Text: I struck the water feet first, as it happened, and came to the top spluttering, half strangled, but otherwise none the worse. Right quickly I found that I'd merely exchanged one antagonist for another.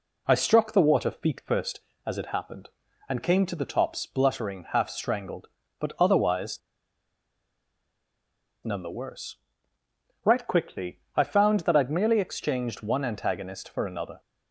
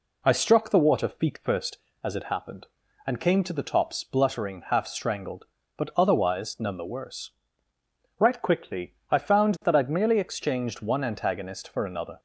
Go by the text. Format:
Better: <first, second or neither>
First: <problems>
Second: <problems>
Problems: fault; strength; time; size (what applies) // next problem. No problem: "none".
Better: second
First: pauses between "otherwise" and "none"; strong; at 6.6 s; 2.0 s long // pauses between "quickly" and "I"; slight; at 10.9 s; 0.16 s long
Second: pauses between "quickly" and "I"; slight; at 8.9 s; 0.16 s long